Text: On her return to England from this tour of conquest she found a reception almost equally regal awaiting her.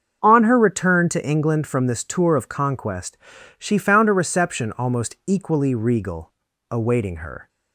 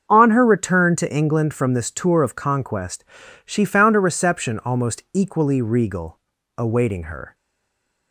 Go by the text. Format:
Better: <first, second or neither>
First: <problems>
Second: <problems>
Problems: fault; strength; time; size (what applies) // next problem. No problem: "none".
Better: first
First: starts louder than the rest; until 1.2 s; 7 dB // pauses between "conquest" and "she"; at 3.1 s; 0.40 s long // pauses between "regal" and "awaiting"; at 6.3 s; 0.38 s long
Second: starts louder than the rest; until 1.1 s; 7 dB // pauses between "conquest" and "she"; at 3.0 s; 0.40 s long // pauses between "regal" and "awaiting"; at 6.1 s; 0.38 s long // stays silent after the last word; slight; from 7.3 s on; 0.8 s long